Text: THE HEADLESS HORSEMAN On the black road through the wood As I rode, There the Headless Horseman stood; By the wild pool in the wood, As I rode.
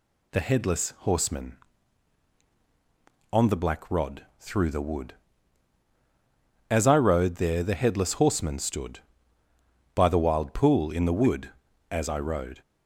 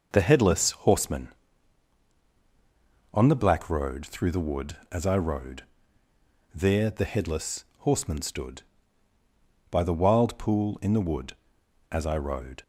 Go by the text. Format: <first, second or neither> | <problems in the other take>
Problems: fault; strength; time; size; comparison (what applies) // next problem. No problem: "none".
second | says "rod" for "road"; at 3.8 s